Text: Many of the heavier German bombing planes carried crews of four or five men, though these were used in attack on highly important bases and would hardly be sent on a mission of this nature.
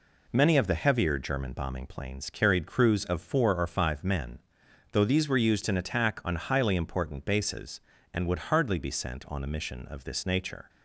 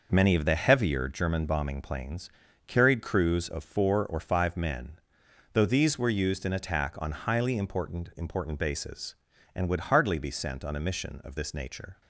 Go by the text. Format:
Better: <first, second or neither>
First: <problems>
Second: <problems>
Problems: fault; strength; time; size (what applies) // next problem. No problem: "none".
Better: first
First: none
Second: pauses between "planes" and "carried"; slight; at 2.3 s; 0.36 s long // says "important" twice; at 8.1 s